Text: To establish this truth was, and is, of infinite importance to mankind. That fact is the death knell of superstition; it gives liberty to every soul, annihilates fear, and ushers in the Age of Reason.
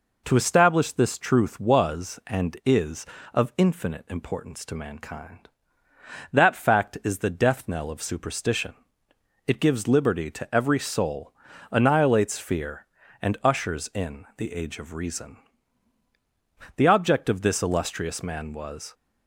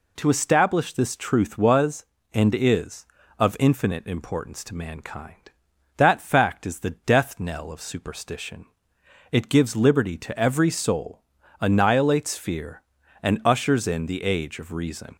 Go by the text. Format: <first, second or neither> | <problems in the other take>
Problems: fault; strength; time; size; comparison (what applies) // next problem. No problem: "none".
second | goes on to say "The object of this illustrious man was"; strong; from 16.7 s on; 2.1 s long